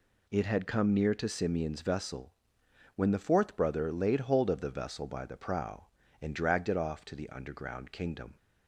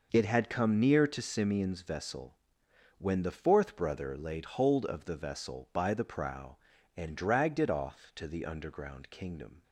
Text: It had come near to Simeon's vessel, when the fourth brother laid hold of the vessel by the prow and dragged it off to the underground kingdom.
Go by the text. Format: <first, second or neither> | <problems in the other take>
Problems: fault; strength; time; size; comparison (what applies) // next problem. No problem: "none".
neither | none